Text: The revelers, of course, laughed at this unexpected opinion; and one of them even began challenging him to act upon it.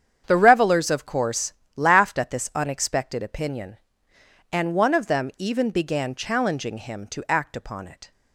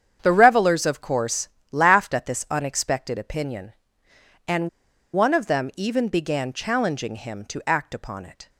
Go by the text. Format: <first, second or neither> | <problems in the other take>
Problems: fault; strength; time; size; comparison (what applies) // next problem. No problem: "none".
first | starts louder than the rest; strong; until 1.2 s; 8 dB; strong in the first // pauses between "and" and "one"; at 4.6 s; 0.45 s long